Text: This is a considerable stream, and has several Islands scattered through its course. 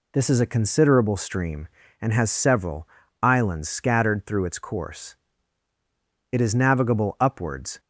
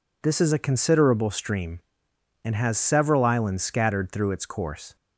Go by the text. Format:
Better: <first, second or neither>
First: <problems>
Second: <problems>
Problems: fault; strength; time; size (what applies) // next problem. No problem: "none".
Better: second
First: pauses between "several" and "Islands"; slight; at 2.8 s; 0.32 s long // goes on to say "It is navigable upwards"; from 6.3 s on; 1.4 s long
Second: none